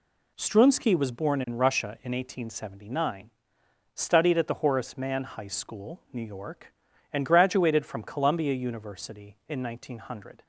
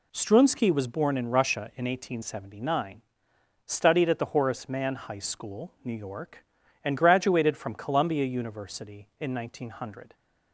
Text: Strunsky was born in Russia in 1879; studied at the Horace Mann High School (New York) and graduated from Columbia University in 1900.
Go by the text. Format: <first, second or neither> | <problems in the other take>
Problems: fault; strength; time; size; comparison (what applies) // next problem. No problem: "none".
neither | none